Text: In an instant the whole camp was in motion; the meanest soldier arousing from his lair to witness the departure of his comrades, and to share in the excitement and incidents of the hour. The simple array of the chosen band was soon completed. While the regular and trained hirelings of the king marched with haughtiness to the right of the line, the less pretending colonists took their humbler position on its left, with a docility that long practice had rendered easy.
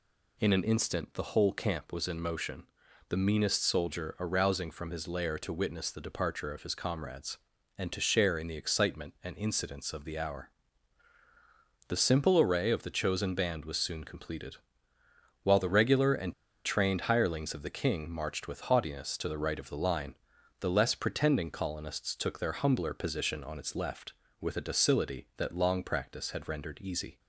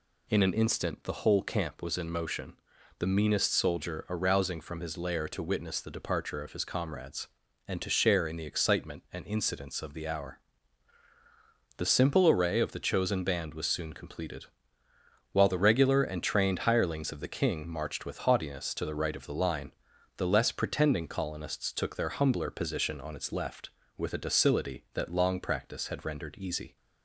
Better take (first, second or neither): second